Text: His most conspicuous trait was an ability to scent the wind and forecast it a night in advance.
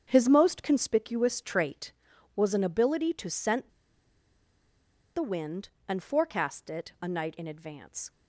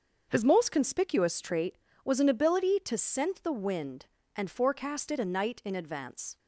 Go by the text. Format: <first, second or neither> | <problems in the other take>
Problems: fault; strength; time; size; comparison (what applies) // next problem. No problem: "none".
second | starts louder than the rest; strong; until 1.0 s; 8 dB; also in the second // pauses between "scent" and "the"; strong; at 3.6 s; 1.4 s long